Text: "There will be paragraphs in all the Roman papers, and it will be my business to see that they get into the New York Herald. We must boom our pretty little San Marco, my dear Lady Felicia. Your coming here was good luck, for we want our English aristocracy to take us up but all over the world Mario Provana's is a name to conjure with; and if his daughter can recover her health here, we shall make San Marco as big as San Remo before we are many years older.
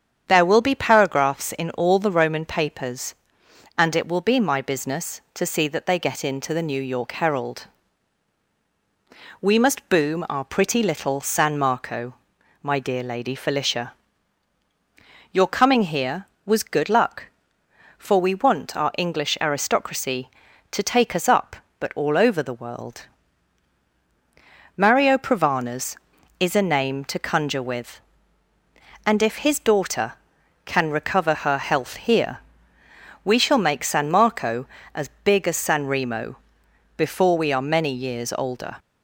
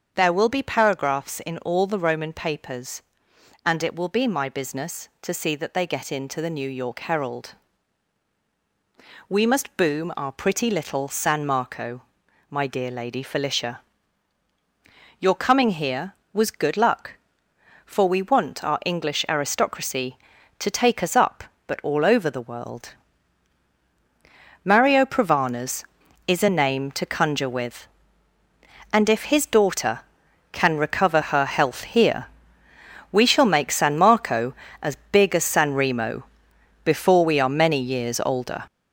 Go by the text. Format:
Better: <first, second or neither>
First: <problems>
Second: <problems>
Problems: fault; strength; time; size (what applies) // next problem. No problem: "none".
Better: first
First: starts louder than the rest; strong; until 1.2 s; 8 dB // pauses between "world" and "Mario"; strong; at 23.0 s; 1.7 s long // pauses between "Remo" and "before"; noticeable; at 36.3 s; 0.60 s long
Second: gets louder; strong; throughout; 7.5 dB // starts louder than the rest; until 1.1 s; 7 dB // pauses between "world" and "Mario"; strong; at 22.9 s; 1.7 s long // pauses between "Remo" and "before"; noticeable; at 36.2 s; 0.60 s long